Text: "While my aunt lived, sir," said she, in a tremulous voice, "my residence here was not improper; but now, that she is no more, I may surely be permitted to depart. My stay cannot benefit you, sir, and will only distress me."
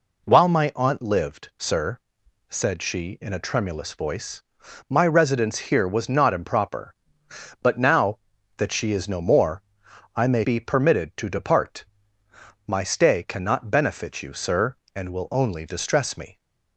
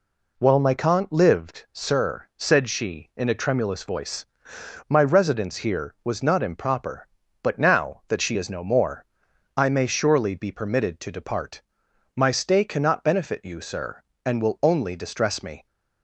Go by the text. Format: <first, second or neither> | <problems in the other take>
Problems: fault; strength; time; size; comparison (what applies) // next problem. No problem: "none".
second | skips "surely"; at 10.4 s